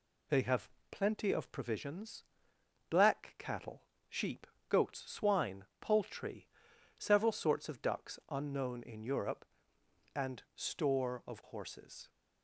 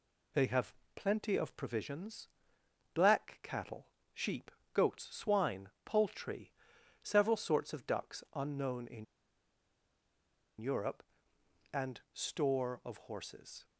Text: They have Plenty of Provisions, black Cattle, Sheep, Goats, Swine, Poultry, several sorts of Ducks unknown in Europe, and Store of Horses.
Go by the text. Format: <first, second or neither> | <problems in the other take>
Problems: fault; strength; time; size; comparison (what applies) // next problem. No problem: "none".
first | pauses between "have" and "Plenty"; slight; at 0.7 s; 0.22 s long; slight in the first // pauses between "in" and "Europe"; strong; at 9.0 s; 1.5 s long